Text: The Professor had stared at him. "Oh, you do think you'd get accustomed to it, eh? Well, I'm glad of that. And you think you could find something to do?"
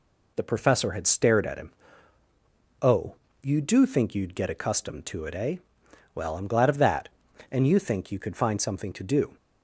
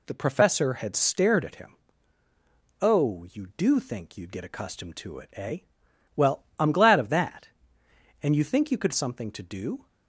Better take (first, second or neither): first